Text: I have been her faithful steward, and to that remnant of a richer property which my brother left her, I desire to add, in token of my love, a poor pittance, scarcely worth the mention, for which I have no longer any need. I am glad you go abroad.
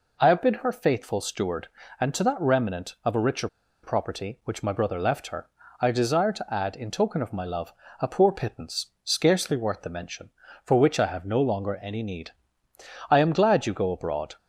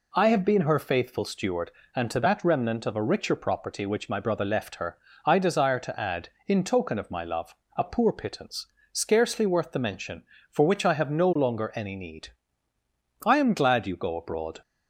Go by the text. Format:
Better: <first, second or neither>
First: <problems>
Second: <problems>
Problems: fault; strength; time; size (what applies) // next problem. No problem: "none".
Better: second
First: pauses between "richer" and "property"; at 3.4 s; 0.36 s long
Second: none